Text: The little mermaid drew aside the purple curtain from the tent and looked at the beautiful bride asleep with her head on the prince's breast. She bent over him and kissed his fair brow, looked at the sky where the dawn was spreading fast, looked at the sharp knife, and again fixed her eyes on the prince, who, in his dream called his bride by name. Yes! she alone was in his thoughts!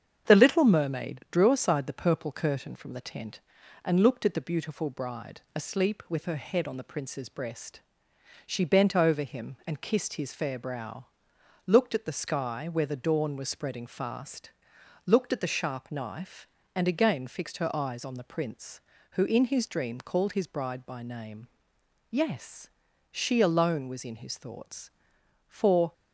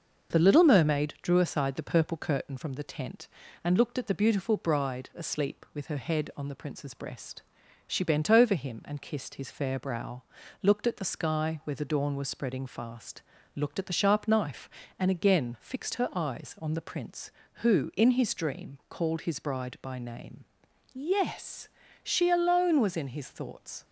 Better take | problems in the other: second | starts louder than the rest; strong; until 1.3 s; 7.5 dB; noticeable in the second // goes on to say "For"; slight; from 25.4 s on; 0.44 s long

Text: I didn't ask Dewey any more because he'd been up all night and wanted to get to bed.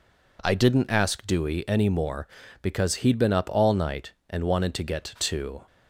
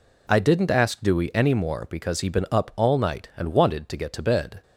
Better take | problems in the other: second | stops before "bed"; at 5.6 s

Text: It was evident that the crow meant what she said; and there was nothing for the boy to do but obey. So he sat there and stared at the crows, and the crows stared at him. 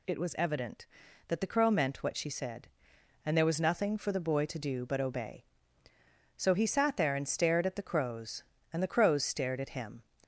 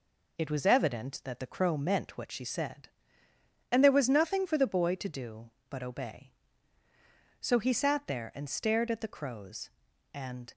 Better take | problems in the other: first | stops before "the crows stared at him"; at 10.5 s

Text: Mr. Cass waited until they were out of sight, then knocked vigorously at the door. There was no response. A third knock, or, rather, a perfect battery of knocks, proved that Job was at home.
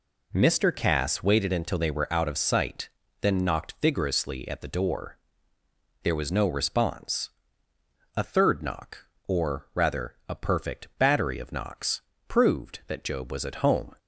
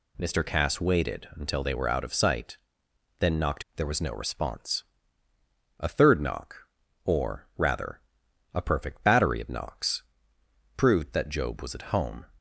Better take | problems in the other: first | skips "vigorously at the door"; at 3.6 s

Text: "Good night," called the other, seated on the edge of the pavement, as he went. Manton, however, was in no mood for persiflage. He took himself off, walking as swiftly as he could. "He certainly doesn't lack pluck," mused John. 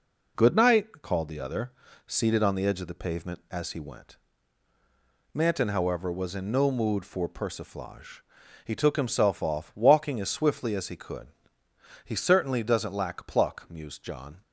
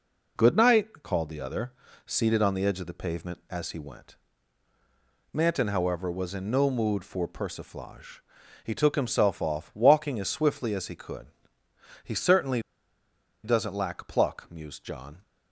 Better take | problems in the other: first | pauses between "certainly" and "doesn't"; noticeable; at 12.6 s; 0.82 s long

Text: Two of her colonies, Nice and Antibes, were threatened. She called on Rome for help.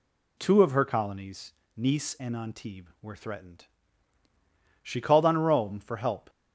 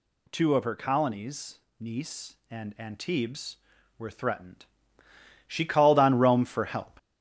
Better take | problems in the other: first | gets louder; noticeable; throughout; 5.5 dB

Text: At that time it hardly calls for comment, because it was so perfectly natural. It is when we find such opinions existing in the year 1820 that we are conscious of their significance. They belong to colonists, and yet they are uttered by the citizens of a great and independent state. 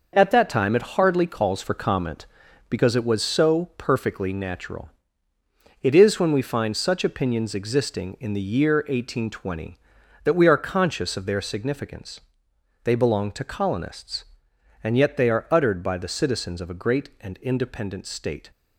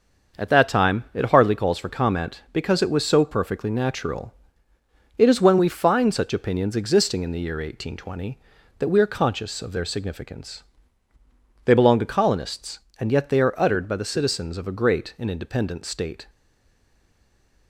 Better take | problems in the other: first | starts louder than the rest; until 1.4 s; 6 dB // stays silent after the last word; noticeable; from 16.2 s on; 1.4 s long

